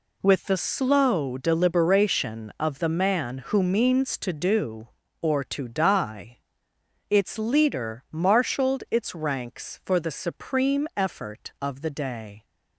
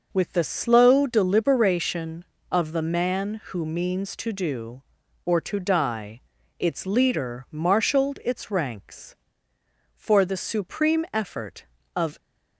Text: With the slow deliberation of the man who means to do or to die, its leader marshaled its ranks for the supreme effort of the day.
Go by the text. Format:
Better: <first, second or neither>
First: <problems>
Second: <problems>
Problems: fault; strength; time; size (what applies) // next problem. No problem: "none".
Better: first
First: none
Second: stops before "the day"; at 12.1 s